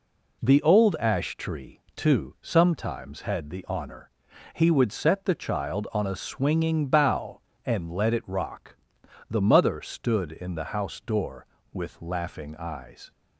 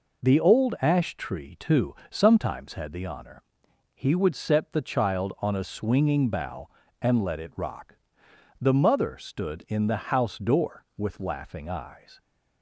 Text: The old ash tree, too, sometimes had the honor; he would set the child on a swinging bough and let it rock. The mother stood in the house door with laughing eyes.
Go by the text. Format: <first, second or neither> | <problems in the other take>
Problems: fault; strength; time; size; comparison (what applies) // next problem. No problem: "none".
neither | none